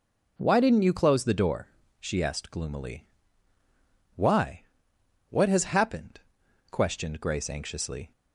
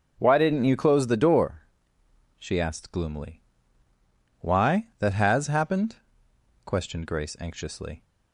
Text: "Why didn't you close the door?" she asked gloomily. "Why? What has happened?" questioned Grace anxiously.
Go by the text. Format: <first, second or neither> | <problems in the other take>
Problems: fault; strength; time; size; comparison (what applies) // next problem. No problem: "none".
first | starts louder than the rest; noticeable; until 1.1 s; 6 dB // says "That" for "What"; at 4.9 s